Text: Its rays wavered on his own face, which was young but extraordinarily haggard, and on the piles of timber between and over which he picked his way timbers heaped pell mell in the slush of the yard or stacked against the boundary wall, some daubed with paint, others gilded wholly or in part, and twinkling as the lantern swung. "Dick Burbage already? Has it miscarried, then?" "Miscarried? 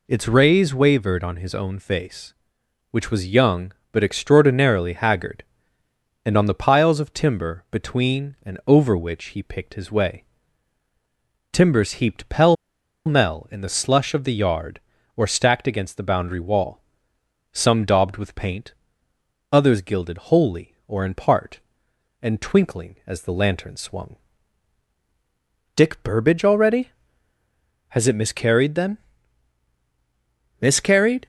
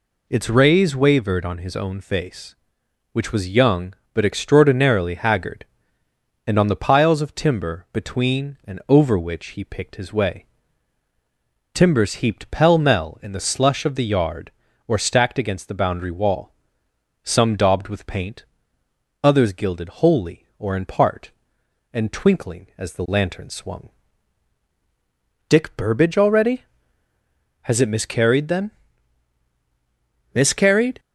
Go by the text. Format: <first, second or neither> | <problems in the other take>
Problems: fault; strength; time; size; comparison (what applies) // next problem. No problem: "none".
second | pauses between "way" and "timbers"; strong; at 10.2 s; 1.2 s long; strong in the second // pauses between "pell" and "mell"; noticeable; at 12.5 s; 0.50 s long